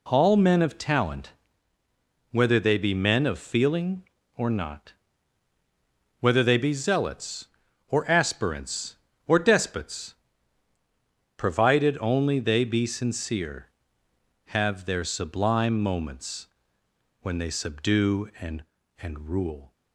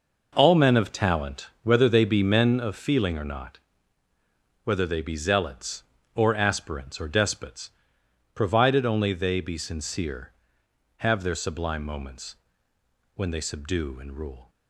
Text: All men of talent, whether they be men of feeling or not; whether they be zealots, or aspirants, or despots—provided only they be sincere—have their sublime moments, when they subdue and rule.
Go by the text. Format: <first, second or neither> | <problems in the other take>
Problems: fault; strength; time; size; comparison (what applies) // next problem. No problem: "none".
second | says "and" twice; at 19.0 s